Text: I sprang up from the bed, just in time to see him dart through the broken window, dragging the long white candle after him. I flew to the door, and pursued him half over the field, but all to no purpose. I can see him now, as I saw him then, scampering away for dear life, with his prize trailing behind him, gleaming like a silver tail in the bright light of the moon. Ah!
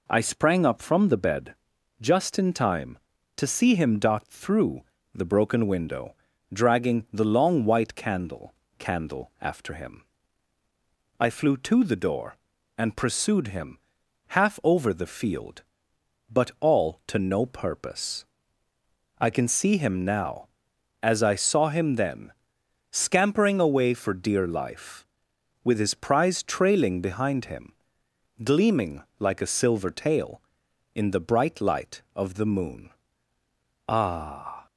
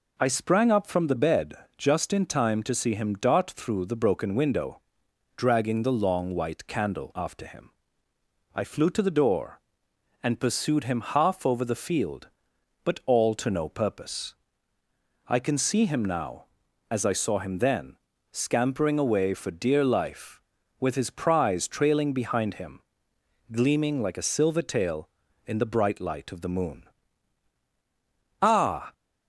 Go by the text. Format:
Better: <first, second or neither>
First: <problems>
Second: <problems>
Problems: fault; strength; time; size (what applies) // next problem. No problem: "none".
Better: second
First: pauses between "through" and "the"; slight; at 4.8 s; 0.30 s long // says "candle" twice; at 8.7 s // pauses between "him" and "half"; noticeable; at 13.7 s; 0.50 s long // pauses between "gleaming" and "like"; slight; at 29.0 s; 0.16 s long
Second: none